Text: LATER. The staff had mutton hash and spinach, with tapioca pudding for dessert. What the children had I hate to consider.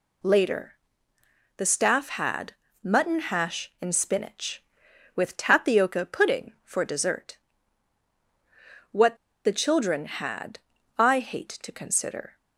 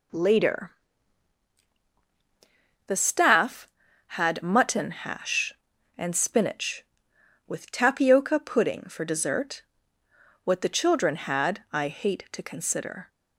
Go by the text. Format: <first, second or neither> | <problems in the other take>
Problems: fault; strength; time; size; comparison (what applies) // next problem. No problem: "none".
second | pauses between "had" and "mutton"; slight; at 2.5 s; 0.30 s long // pauses between "What" and "the"; slight; at 9.1 s; 0.29 s long // pauses between "had" and "I"; at 10.5 s; 0.38 s long